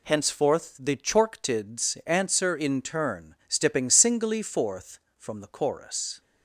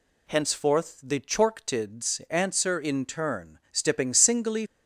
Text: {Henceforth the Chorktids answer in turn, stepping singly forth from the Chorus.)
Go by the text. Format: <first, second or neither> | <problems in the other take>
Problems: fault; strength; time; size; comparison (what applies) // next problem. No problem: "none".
first | stops before "forth from the Chorus"; at 4.6 s